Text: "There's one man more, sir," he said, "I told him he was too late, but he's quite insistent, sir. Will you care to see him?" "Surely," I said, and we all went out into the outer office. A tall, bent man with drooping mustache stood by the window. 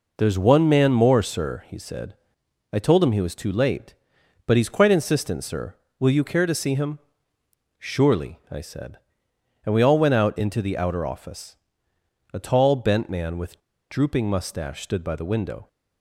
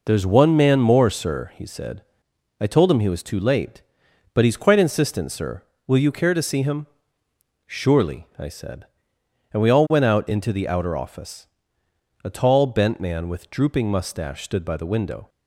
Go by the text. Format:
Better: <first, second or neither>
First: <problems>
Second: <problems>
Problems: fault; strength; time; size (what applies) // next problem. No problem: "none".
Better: second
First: pauses between "with" and "drooping"; slight; at 13.5 s; 0.30 s long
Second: none